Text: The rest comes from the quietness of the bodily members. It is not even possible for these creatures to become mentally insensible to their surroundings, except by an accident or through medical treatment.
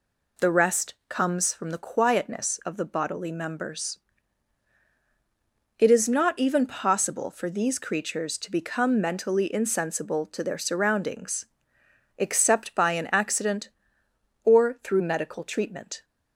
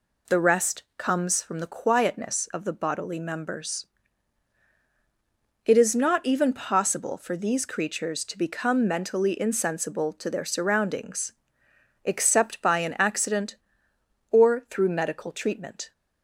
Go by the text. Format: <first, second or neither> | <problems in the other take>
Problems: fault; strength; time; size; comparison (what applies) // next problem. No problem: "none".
neither | none